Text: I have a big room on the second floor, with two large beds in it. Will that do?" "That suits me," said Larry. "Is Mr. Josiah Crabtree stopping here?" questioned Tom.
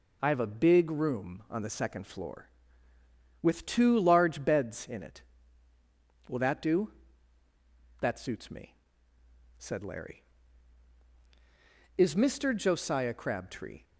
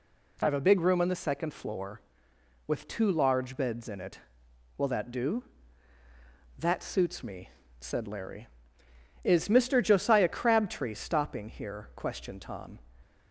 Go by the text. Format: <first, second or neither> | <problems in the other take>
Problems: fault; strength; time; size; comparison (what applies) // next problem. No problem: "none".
second | stops before "stopping here questioned Tom"; at 13.8 s